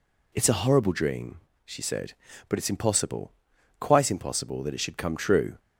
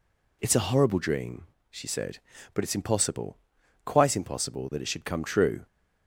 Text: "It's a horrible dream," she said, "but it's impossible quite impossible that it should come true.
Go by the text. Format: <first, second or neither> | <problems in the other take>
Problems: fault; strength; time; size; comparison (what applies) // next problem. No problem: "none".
neither | pauses between "impossible" and "quite"; noticeable; the same in both